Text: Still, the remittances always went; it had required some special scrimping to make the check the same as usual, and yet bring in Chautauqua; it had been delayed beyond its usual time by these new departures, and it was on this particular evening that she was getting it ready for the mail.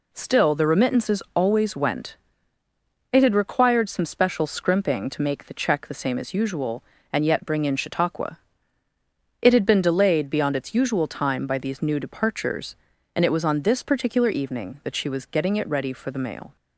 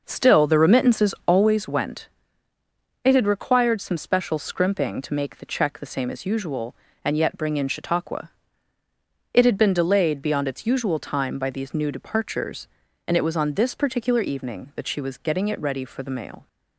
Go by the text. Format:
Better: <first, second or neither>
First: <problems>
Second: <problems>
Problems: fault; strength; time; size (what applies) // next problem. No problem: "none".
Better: first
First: none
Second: starts louder than the rest; noticeable; until 1.7 s; 5.5 dB